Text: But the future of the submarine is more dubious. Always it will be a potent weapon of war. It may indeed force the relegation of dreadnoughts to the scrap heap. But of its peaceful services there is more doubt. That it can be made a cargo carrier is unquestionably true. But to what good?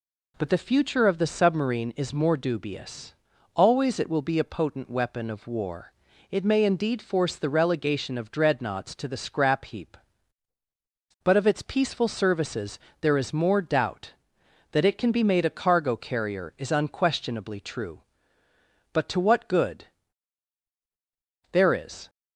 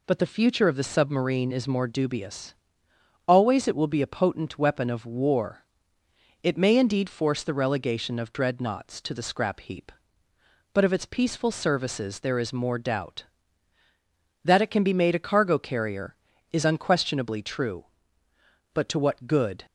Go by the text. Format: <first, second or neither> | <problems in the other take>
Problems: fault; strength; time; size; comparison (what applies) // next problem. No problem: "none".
second | pauses between "services" and "there"; slight; at 12.7 s; 0.24 s long // goes on to say "There is"; from 21.5 s on; 0.56 s long